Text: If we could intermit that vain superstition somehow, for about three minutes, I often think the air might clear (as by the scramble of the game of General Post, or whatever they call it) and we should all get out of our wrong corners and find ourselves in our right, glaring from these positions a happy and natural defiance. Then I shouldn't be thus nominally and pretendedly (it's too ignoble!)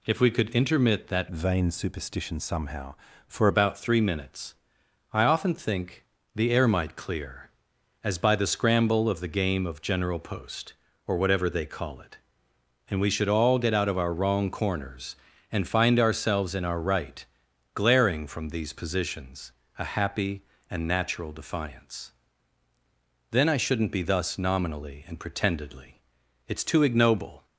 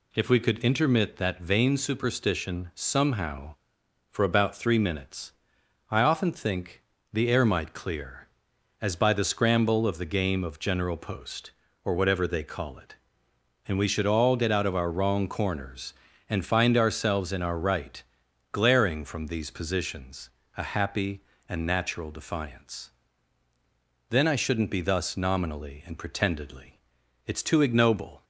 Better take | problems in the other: second | changes voice from "vain" to "for"; from 1.3 to 3.4 s; 2.1 s long // pauses between "think" and "the"; slight; at 6.0 s; 0.30 s long; slight in the second // pauses between "positions" and "a"; slight; at 19.5 s; 0.28 s long; slight in the second

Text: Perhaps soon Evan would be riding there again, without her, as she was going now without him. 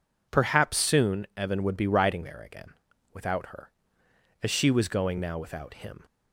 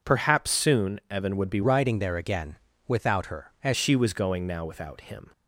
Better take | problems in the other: first | changes voice from "riding" to "as"; from 1.6 to 3.7 s; 2.1 s long

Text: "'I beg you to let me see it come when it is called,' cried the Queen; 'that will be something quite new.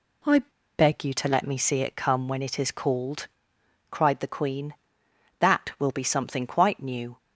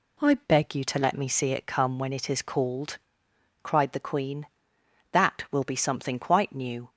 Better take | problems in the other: second | pauses between "I" and "beg"; at 0.3 s; 0.38 s long

